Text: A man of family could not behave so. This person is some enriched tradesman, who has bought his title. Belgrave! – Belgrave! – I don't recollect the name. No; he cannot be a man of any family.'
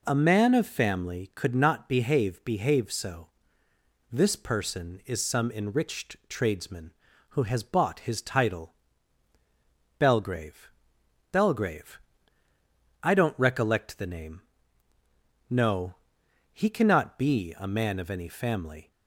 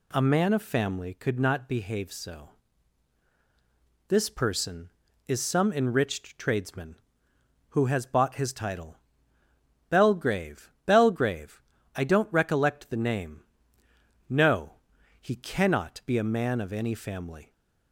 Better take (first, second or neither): second